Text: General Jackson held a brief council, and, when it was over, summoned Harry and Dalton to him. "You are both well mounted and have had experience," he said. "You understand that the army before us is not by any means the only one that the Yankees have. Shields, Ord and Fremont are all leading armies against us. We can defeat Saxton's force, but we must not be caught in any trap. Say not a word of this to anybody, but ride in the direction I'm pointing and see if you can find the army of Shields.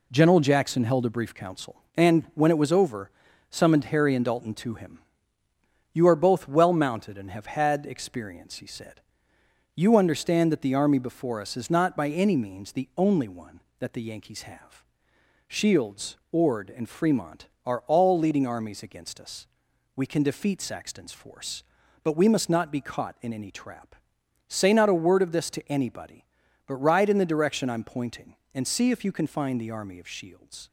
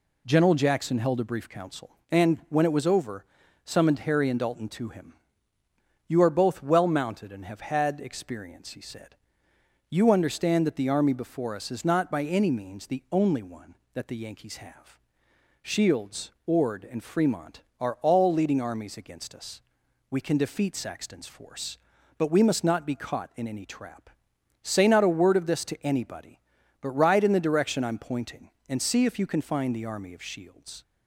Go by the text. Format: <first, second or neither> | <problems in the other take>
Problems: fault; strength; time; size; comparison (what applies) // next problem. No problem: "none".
second | gets quieter; noticeable; throughout; 5.5 dB